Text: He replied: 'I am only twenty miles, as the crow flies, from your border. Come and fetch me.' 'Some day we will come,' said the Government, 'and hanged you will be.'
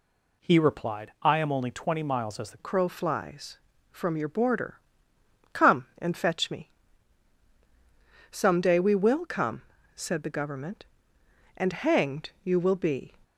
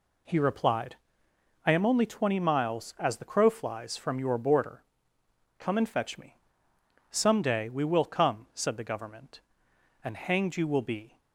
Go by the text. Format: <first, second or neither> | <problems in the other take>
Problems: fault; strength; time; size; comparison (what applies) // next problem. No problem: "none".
second | changes voice at "crow"; from 2.5 s on; 10.6 s long